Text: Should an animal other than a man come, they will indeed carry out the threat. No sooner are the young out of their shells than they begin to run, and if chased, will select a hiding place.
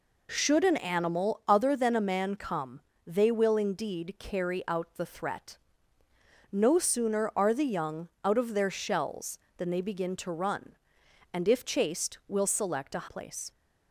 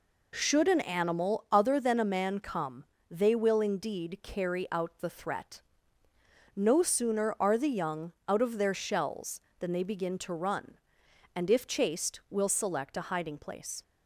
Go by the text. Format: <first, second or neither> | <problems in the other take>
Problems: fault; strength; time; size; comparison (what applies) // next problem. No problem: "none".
second | skips "hiding"; at 13.0 s